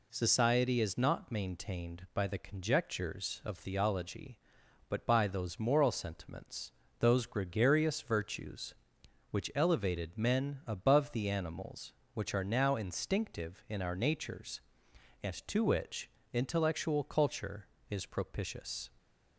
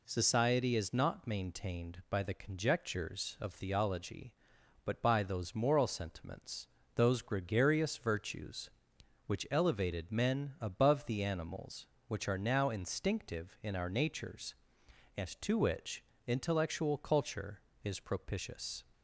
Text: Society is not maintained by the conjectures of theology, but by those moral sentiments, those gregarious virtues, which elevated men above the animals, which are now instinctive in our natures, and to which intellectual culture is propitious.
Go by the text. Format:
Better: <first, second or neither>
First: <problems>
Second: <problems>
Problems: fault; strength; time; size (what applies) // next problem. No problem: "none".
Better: neither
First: pauses between "which" and "intellectual"; slight; at 16.0 s; 0.24 s long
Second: pauses between "which" and "intellectual"; slight; at 16.0 s; 0.24 s long